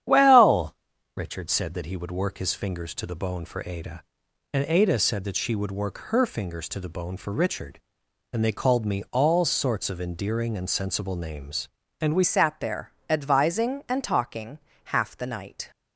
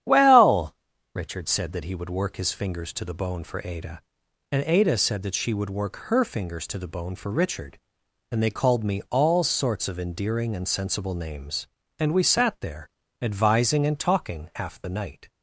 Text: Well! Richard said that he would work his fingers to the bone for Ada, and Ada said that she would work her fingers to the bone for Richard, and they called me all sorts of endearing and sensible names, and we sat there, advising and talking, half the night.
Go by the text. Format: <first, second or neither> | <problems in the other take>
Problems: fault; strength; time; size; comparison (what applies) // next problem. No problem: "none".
second | starts louder than the rest; strong; until 1.4 s; 10 dB; strong in the second // changes voice at "sat"; from 12.2 s on; 3.5 s long